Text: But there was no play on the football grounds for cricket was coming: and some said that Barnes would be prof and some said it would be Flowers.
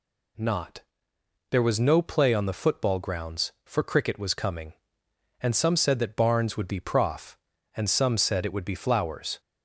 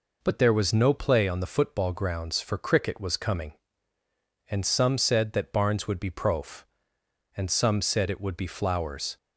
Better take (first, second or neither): second